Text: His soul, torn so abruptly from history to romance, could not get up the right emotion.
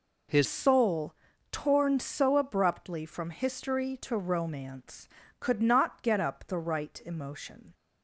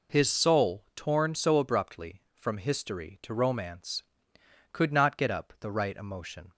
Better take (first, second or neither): second